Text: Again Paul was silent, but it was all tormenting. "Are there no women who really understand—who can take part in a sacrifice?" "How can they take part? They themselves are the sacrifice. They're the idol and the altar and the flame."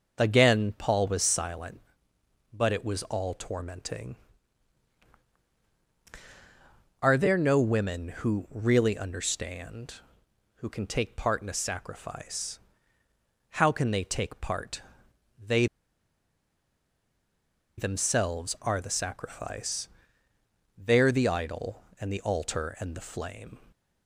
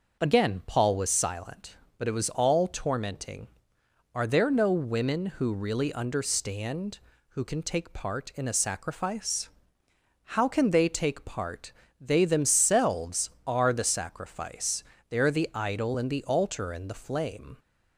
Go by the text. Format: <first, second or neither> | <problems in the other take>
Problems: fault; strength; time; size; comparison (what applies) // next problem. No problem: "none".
second | pauses between "They" and "themselves"; strong; at 15.6 s; 2.1 s long